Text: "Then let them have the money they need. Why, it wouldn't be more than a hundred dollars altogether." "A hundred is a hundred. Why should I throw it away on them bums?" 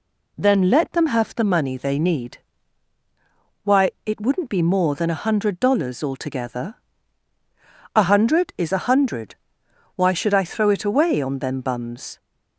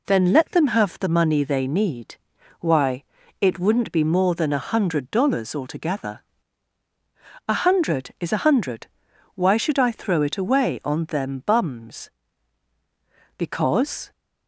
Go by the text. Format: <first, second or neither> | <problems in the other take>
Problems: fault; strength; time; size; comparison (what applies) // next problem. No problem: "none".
first | goes on to say "Because"; noticeable; from 13.3 s on; 0.74 s long